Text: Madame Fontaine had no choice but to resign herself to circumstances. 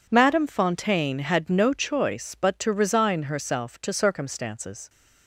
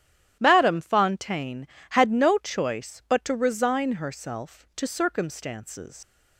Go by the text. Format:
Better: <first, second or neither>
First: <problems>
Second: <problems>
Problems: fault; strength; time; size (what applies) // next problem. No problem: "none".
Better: first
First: none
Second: starts louder than the rest; strong; until 1.4 s; 11 dB // leaves "circumstances" unfinished; at 6.0 s; 110 ms